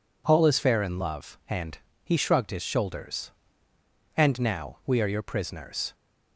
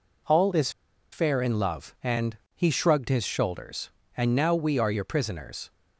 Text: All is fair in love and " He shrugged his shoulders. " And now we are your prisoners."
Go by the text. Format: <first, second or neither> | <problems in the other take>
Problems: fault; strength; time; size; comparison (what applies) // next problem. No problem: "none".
first | pauses between "is" and "fair"; at 0.6 s; 0.42 s long